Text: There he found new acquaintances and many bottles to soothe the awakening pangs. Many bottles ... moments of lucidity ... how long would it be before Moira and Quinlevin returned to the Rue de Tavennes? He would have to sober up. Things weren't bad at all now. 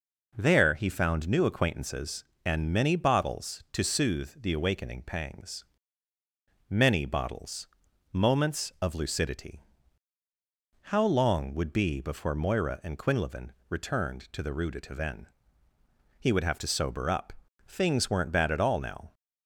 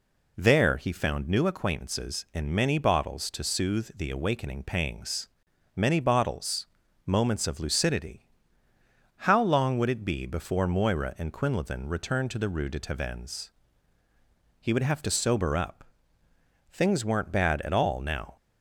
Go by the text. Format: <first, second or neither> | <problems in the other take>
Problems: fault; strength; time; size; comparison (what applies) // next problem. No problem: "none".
second | skips "it"; at 11.7 s // pauses between "Quinlevin" and "returned"; slight; at 13.4 s; 0.20 s long